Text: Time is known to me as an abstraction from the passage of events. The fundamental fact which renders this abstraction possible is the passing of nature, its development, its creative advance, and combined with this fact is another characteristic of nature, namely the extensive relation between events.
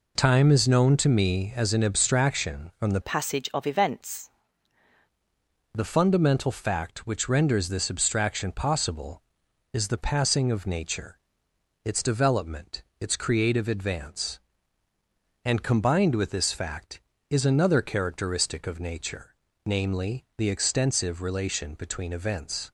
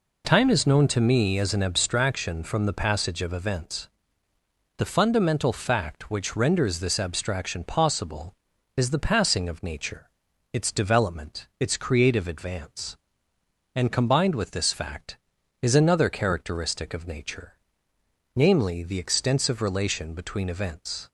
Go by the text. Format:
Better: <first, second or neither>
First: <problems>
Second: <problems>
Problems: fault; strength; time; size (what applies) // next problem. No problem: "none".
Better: second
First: changes voice from "passage" to "events"; from 3.0 to 4.2 s; 1.2 s long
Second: none